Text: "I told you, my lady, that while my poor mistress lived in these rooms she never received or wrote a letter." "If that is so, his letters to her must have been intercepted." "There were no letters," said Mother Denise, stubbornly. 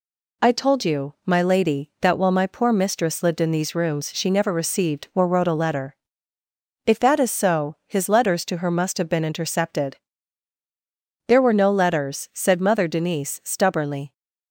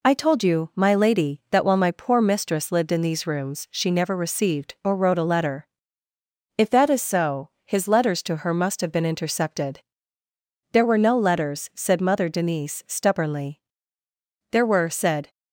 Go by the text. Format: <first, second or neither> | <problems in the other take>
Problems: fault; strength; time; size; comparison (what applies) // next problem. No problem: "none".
first | goes on to say "There were said"; noticeable; from 14.5 s on; 0.78 s long